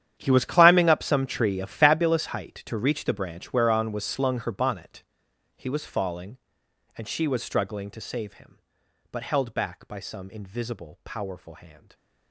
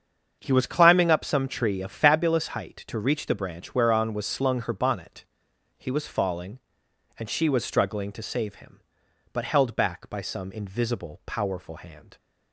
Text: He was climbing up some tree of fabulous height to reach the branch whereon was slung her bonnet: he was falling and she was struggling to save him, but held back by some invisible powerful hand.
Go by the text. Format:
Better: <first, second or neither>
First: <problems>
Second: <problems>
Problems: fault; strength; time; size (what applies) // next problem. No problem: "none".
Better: second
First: gets quieter; strong; throughout; 16.5 dB // starts louder than the rest; strong; until 1.1 s; 10 dB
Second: starts louder than the rest; strong; until 1.4 s; 7.5 dB